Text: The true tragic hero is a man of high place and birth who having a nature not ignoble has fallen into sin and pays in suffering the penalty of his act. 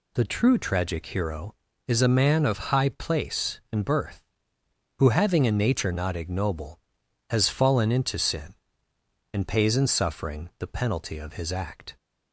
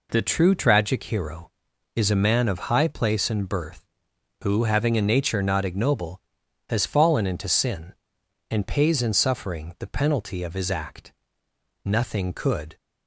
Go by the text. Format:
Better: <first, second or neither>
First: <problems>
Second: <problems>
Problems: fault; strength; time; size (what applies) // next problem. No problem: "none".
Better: first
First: none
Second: goes on to say "Nothing could"; noticeable; from 11.8 s on; 0.92 s long